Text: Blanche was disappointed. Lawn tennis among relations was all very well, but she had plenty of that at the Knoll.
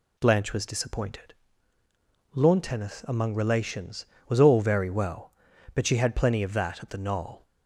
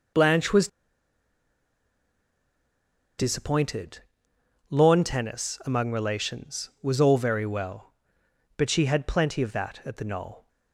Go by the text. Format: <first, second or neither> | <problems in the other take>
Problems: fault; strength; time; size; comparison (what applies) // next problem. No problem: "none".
first | pauses between "was" and "disappointed"; strong; at 0.6 s; 2.5 s long